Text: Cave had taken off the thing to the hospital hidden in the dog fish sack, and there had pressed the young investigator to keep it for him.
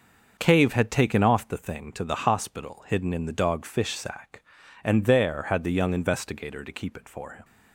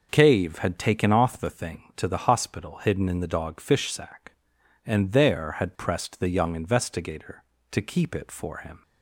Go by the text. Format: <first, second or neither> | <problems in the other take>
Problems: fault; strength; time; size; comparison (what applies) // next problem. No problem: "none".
second | starts louder than the rest; until 1.4 s; 6.5 dB // skips "pressed"; at 5.6 s